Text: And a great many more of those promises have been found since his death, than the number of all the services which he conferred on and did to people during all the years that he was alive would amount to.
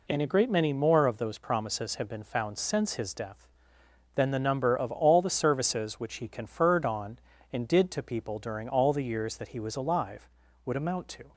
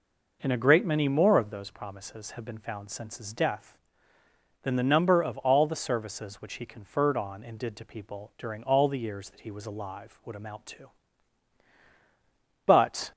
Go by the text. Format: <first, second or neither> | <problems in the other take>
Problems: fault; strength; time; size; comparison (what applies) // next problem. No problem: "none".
first | goes on to say "But"; slight; from 12.6 s on; 0.46 s long